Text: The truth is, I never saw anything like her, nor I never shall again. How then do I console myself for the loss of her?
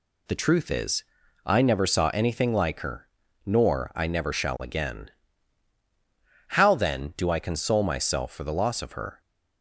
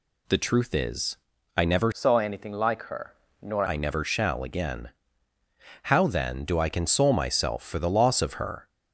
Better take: first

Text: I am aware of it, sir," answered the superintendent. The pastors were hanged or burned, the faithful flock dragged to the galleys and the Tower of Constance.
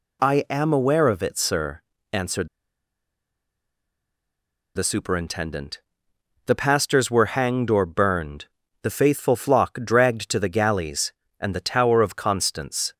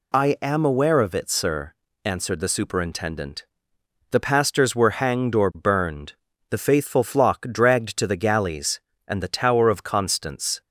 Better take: second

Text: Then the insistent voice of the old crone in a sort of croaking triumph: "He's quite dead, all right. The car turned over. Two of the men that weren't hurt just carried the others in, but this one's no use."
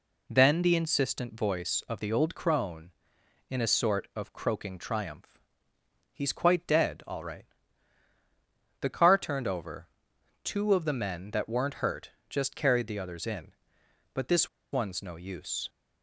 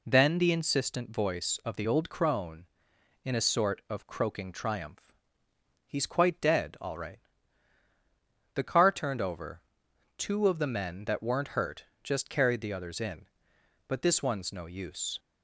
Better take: second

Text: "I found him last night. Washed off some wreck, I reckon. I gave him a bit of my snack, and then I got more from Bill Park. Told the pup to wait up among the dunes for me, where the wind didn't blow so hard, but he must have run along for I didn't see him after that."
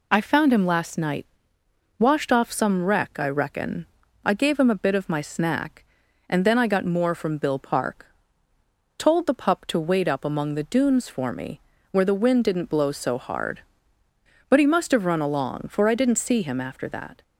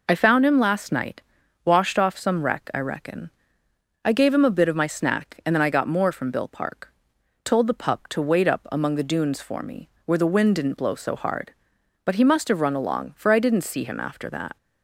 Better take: neither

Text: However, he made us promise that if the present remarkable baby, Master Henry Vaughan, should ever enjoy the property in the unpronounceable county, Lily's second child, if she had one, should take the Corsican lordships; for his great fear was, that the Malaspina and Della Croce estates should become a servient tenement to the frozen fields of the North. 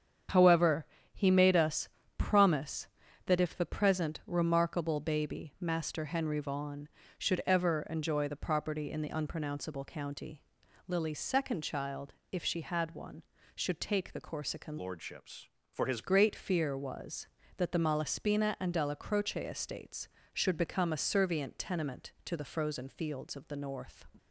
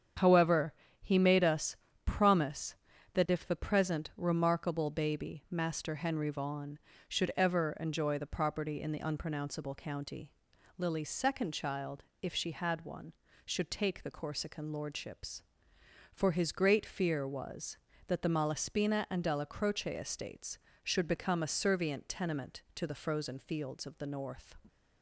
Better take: second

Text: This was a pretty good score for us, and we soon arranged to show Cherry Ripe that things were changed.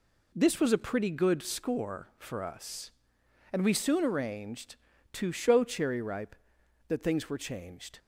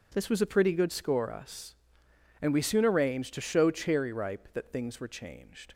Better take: first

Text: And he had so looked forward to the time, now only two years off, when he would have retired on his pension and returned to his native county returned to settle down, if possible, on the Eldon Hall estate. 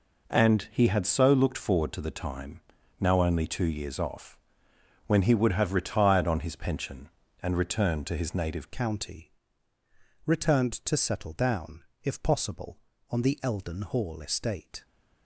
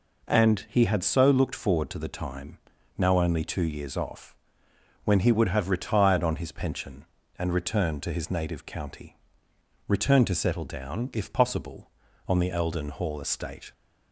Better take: second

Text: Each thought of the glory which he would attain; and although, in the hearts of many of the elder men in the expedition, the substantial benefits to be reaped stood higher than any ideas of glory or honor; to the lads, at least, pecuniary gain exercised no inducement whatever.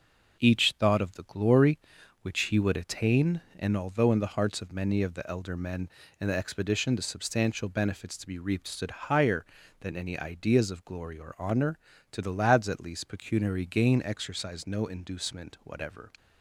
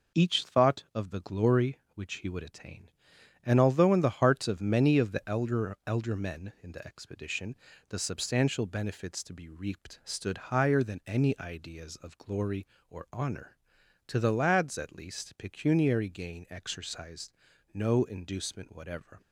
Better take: first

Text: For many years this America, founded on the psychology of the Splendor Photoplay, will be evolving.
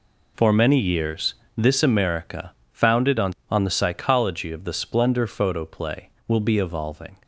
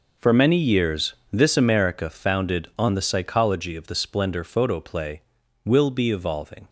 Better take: second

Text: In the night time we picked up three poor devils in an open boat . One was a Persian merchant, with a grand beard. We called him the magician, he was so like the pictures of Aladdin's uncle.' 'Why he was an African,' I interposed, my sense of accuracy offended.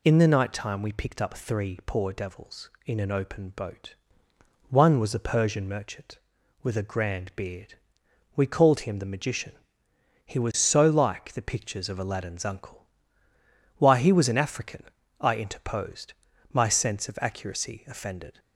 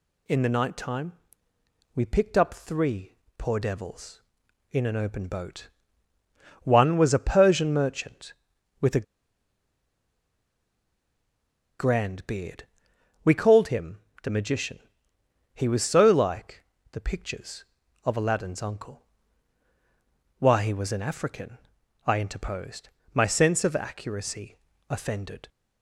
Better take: first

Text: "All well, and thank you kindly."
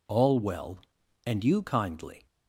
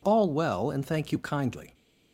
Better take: second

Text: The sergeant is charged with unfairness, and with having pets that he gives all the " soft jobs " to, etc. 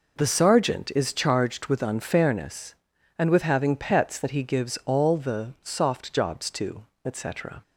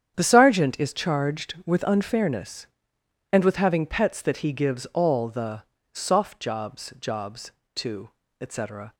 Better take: first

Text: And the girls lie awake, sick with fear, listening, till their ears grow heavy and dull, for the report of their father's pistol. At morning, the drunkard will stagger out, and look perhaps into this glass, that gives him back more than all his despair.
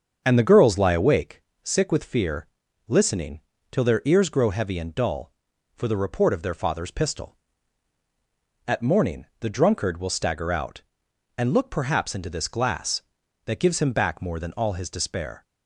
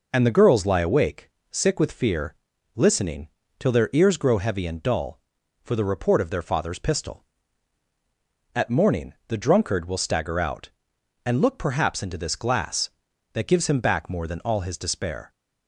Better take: second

